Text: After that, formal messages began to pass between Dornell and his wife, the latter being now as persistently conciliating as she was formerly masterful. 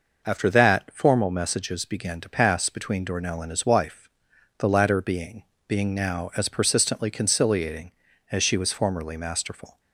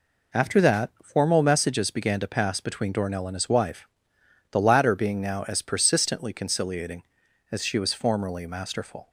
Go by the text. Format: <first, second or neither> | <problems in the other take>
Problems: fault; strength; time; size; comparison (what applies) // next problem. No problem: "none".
second | says "being" twice; at 5.6 s